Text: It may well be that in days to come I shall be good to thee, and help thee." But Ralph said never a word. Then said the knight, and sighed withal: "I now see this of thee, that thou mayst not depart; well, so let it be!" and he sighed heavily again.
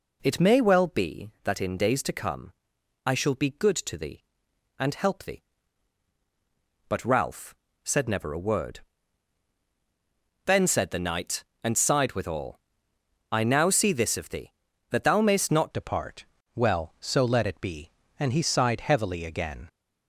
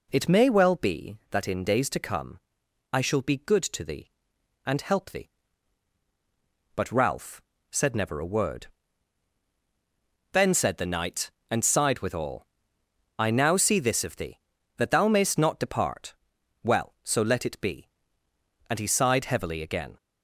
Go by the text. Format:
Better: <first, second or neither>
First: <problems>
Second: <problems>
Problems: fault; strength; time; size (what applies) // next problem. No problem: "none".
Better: second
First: pauses between "come" and "I"; noticeable; at 2.5 s; 0.54 s long // pauses between "Ralph" and "said"; slight; at 7.5 s; 0.30 s long // changes voice at "depart"; from 15.7 s on; 3.9 s long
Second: pauses between "come" and "I"; noticeable; at 2.3 s; 0.54 s long // pauses between "Ralph" and "said"; slight; at 7.4 s; 0.30 s long